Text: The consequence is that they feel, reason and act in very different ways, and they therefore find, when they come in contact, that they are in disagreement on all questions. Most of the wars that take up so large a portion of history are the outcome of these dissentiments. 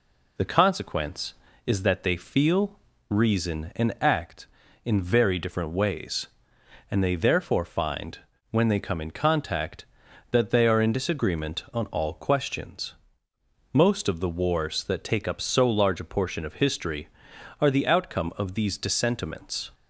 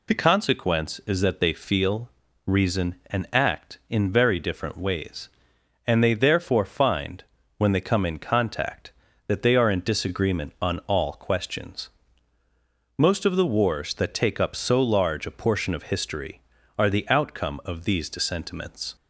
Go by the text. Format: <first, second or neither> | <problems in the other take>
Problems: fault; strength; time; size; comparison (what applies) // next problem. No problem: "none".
neither | none